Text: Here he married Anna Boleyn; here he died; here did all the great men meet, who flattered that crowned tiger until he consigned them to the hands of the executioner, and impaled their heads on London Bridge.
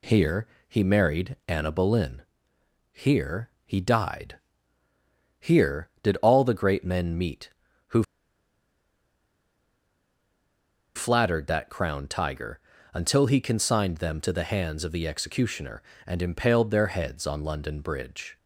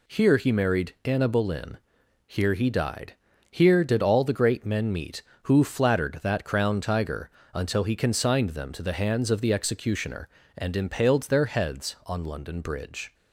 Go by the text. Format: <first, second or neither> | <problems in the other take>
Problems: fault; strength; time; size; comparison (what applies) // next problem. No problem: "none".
second | pauses between "Here" and "he"; slight; at 0.4 s; 0.22 s long // pauses between "here" and "he"; slight; at 3.4 s; 0.16 s long // pauses between "who" and "flattered"; strong; at 8.0 s; 2.9 s long // pauses between "tiger" and "until"; slight; at 12.6 s; 0.32 s long; slight in the second